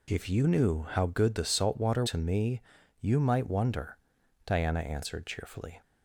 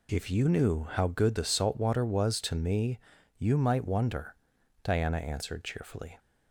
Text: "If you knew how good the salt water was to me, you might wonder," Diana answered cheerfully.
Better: second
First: skips "was"; at 2.0 s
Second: none

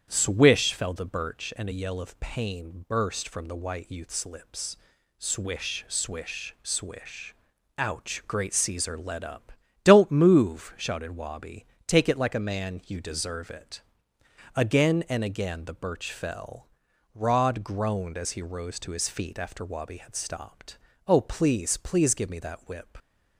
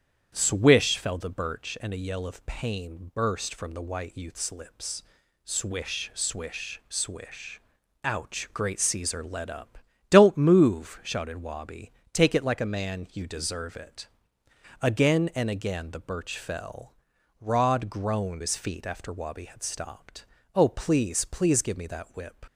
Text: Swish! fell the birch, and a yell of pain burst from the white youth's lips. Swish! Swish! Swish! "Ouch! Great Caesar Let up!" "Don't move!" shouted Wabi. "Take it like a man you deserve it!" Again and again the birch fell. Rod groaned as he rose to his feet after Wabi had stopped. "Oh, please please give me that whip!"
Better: first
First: starts louder than the rest; strong; until 1.0 s; 9 dB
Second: starts louder than the rest; strong; until 1.3 s; 9 dB // skips "as he rose to"; at 18.4 s

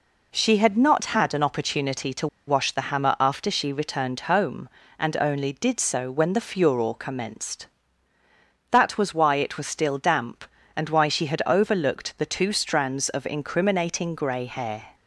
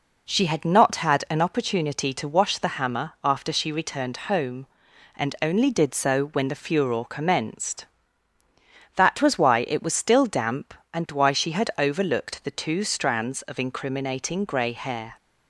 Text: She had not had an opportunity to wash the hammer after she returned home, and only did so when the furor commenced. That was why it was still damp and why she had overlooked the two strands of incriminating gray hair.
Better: second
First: pauses between "to" and "wash"; slight; at 2.2 s; 0.20 s long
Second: none

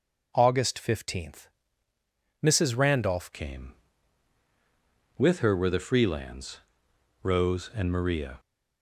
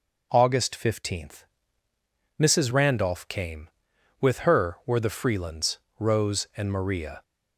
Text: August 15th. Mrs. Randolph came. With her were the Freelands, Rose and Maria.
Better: second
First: changes voice at "came"; from 3.3 s on; 5.0 s long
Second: none

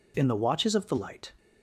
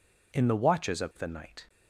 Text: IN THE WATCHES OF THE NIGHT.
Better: second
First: says "Light" for "NIGHT"; at 0.9 s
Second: none

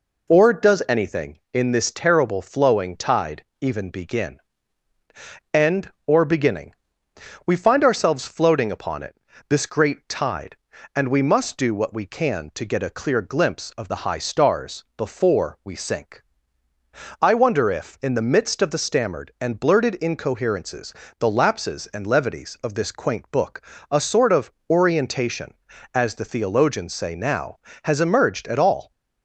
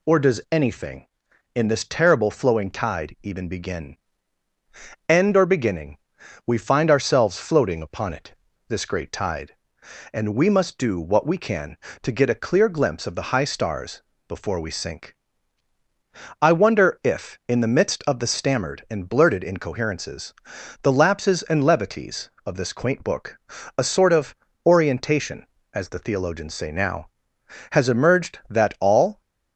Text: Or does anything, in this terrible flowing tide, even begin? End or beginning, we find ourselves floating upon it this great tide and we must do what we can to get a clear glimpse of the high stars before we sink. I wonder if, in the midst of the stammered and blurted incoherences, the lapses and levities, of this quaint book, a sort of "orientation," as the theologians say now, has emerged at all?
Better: first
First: pauses between "it" and "this"; slight; at 9.1 s; 0.32 s long // pauses between "of" and "orientation"; slight; at 24.5 s; 0.16 s long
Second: pauses between "it" and "this"; slight; at 8.3 s; 0.32 s long // pauses between "stars" and "before"; slight; at 14.0 s; 0.28 s long // pauses between "of" and "orientation"; slight; at 24.3 s; 0.28 s long // says "that" for "at"; at 28.4 s

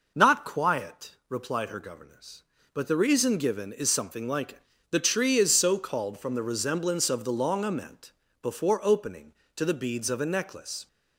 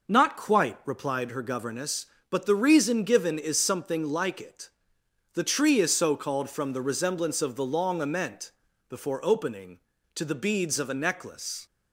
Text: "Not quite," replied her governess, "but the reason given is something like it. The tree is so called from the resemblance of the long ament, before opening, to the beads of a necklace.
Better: second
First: says "quiet" for "quite"; at 0.4 s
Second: none

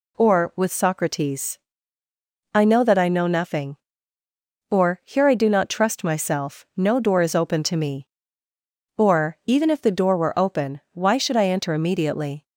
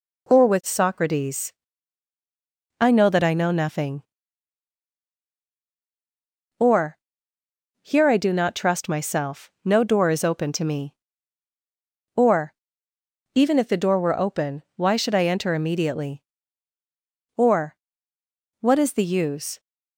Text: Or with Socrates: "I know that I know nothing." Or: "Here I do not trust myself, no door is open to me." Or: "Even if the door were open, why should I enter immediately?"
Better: first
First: none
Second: goes on to say "Or What is the use"; strong; from 17.3 s on; 2.2 s long

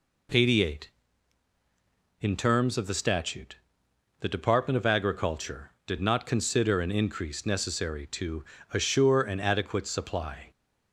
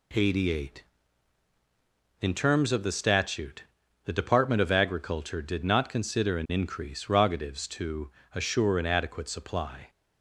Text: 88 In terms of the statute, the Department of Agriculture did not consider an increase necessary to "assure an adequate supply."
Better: first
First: pauses between "to" and "assure"; slight; at 8.4 s; 0.28 s long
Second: says "rogatives" for "necessary"; at 7.0 s // pauses between "to" and "assure"; slight; at 8.1 s; 0.22 s long

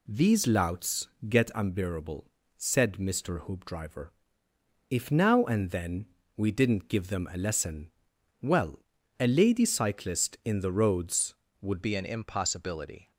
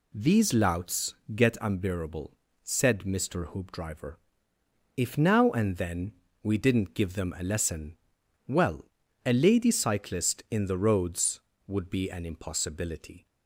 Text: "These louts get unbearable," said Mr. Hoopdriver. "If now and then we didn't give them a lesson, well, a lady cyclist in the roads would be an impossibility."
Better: second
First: pauses between "louts" and "get"; slight; at 1.0 s; 0.22 s long // pauses between "then" and "we"; slight; at 6.0 s; 0.28 s long // changes voice at "be"; from 11.8 s on; 1.3 s long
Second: pauses between "louts" and "get"; slight; at 1.1 s; 0.22 s long // pauses between "then" and "we"; slight; at 6.1 s; 0.28 s long

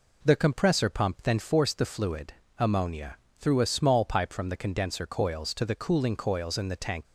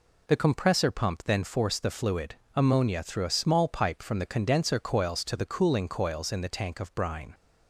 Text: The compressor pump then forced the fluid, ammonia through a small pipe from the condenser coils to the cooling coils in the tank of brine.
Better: second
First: pauses between "ammonia" and "through"; slight; at 3.1 s; 0.24 s long // stops before "of brine"; at 7.0 s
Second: none

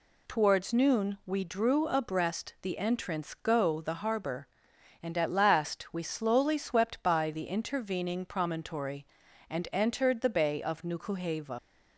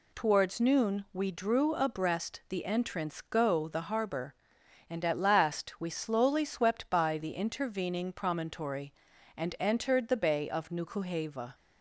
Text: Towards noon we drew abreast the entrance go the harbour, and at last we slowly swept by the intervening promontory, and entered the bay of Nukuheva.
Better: second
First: leaves "Nukuheva" unfinished; at 11.5 s; 90 ms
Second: none

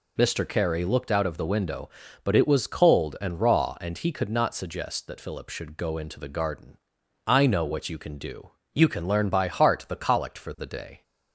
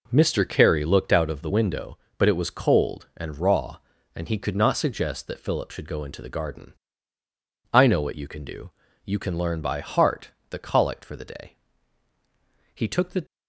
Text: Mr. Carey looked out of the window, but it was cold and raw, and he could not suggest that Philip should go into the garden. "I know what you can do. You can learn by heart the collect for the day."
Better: first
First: none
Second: pauses between "heart" and "the"; slight; at 10.3 s; 0.20 s long // goes on to say "He took the"; from 12.7 s on; 0.50 s long

